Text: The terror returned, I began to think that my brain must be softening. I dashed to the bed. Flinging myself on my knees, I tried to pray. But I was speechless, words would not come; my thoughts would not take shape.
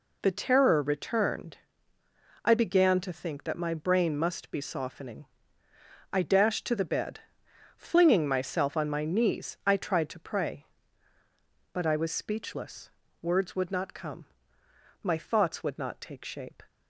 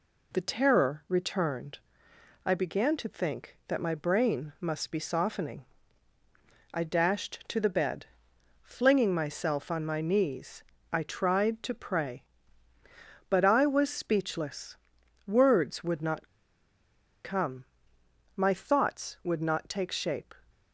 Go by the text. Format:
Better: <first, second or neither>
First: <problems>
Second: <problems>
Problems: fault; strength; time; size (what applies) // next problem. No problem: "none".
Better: first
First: none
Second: pauses between "not" and "come"; noticeable; at 16.2 s; 0.95 s long